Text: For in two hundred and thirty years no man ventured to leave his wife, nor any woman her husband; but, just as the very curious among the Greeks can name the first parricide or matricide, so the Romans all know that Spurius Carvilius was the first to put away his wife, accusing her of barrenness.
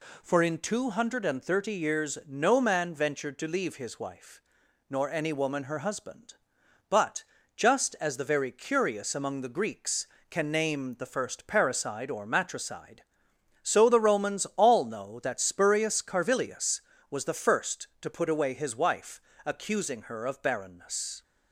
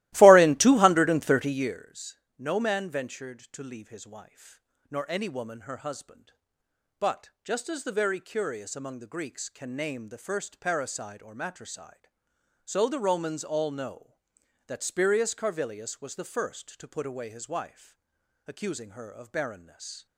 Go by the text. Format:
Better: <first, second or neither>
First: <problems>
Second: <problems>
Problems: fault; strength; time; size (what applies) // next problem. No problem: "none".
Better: first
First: none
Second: starts louder than the rest; strong; until 1.8 s; 17 dB // pauses between "years" and "no"; slight; at 2.1 s; 0.20 s long